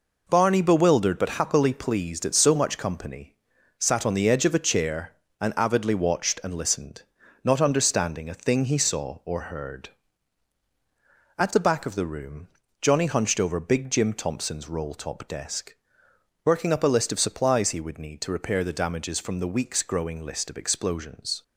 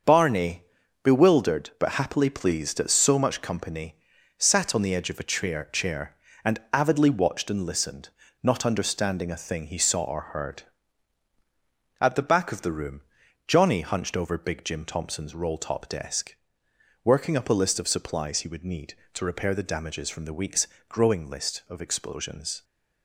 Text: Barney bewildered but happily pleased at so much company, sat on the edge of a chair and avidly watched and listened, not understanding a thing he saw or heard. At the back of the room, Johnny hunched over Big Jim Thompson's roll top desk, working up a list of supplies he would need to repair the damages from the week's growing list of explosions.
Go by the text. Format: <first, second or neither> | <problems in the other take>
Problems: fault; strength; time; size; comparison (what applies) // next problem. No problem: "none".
first | starts louder than the rest; until 1.4 s; 6.5 dB // pauses between "Barney" and "bewildered"; at 0.6 s; 0.38 s long // says "chair" twice; at 5.7 s // pauses between "week's" and "growing"; slight; at 20.6 s; 0.22 s long